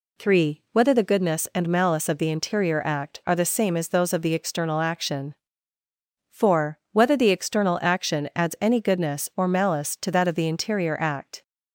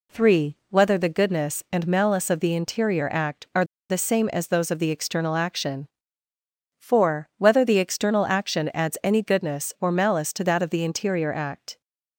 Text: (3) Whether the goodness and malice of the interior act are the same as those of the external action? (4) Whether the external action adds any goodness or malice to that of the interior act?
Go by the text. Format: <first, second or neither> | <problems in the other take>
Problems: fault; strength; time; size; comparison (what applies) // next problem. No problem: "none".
first | pauses between "are" and "the"; slight; at 3.6 s; 0.26 s long